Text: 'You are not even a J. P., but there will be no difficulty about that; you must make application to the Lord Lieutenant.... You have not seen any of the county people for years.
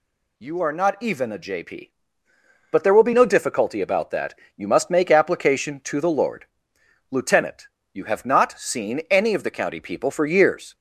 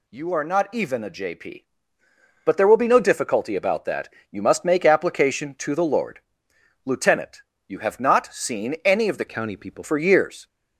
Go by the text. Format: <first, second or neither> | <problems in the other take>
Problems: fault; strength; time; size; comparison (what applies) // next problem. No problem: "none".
first | pauses between "Lord" and "Lieutenant"; noticeable; at 6.2 s; 0.64 s long; noticeable in the first // changes voice from "county" to "people"; from 9.2 to 9.8 s; 0.6 s long